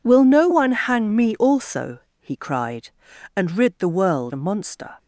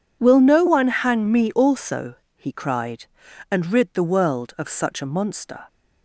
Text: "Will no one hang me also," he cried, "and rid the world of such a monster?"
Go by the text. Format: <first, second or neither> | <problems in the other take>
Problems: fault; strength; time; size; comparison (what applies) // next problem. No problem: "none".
second | skips "of such"; at 4.3 s